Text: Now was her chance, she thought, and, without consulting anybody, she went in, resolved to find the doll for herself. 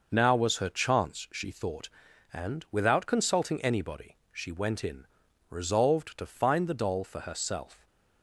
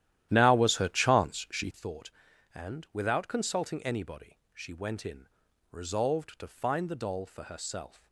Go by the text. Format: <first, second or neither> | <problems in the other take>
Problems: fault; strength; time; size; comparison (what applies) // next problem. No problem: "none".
first | starts louder than the rest; strong; until 1.9 s; 12.5 dB